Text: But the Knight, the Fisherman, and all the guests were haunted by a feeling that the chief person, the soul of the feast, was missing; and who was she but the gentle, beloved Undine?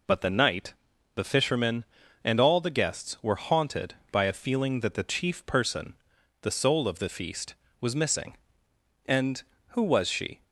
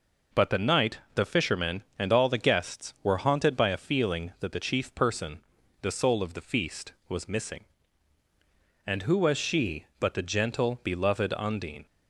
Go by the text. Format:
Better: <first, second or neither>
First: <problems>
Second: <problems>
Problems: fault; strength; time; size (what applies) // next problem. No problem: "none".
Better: second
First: stops before "but the gentle beloved Undine"; at 10.4 s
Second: none